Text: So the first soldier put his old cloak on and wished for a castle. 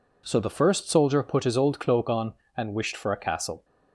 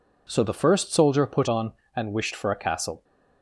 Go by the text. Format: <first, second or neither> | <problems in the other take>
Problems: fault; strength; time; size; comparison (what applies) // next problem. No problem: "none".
first | skips "his old cloak"; at 1.4 s